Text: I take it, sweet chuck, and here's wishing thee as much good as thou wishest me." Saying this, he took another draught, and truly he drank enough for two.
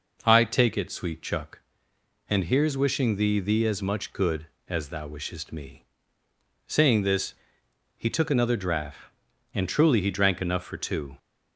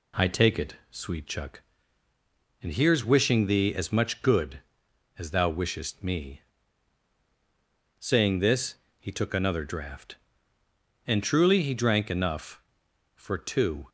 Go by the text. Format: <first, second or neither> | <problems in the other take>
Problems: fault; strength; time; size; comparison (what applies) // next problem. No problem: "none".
second | says "thee" twice; at 3.3 s